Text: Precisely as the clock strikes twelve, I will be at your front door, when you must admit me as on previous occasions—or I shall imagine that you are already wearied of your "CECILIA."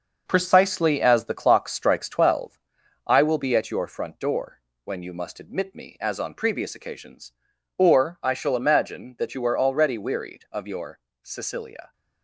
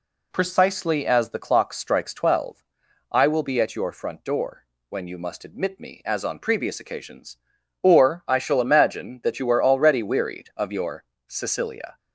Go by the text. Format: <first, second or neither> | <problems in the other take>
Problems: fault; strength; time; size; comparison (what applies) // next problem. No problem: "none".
second | gets quieter; throughout; 6.5 dB // pauses between "your" and "CECILIA"; slight; at 10.9 s; 0.24 s long; slight in the second